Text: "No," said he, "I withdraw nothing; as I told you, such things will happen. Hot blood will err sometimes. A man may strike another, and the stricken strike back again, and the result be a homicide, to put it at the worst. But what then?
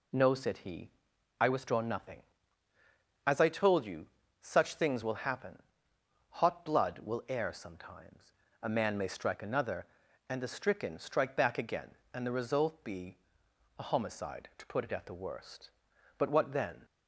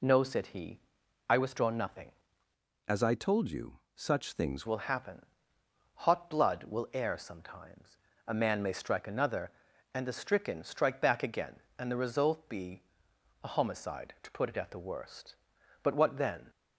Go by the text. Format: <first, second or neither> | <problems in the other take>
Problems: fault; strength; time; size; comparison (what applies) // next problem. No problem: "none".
first | changes voice from "as" to "things"; from 2.8 to 4.6 s; 1.8 s long // pauses between "be" and "a"; noticeable; at 12.8 s; 0.62 s long; noticeable in the first